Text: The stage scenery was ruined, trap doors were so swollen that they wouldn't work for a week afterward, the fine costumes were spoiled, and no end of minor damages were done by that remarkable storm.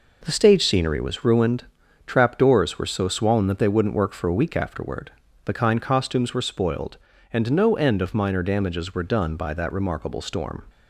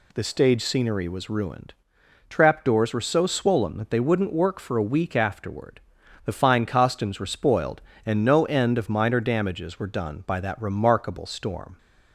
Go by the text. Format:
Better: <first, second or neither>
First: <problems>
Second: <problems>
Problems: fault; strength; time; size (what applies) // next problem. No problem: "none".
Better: second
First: says "kind" for "fine"; at 5.5 s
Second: none